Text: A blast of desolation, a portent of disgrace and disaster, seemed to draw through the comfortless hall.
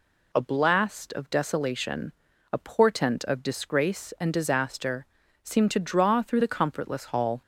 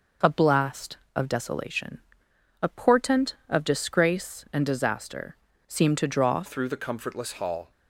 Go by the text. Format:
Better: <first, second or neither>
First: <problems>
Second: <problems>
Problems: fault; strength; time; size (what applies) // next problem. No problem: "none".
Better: first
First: none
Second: changes voice at "through"; from 6.4 s on; 1.3 s long